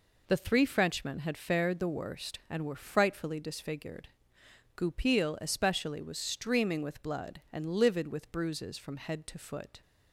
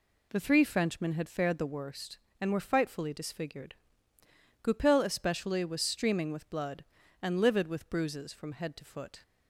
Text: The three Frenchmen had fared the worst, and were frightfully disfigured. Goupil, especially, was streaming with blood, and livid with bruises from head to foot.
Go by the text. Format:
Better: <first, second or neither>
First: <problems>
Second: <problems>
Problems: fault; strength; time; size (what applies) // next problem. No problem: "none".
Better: neither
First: none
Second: none